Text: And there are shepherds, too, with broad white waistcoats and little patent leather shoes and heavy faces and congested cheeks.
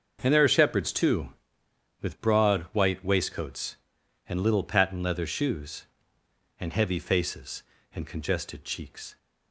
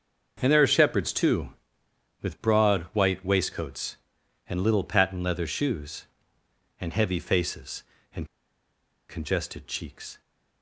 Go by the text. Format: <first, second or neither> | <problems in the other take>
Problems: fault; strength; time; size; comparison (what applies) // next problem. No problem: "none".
first | starts louder than the rest; until 1.4 s; 6.5 dB; also in the first // pauses between "and" and "congested"; noticeable; at 8.2 s; 0.84 s long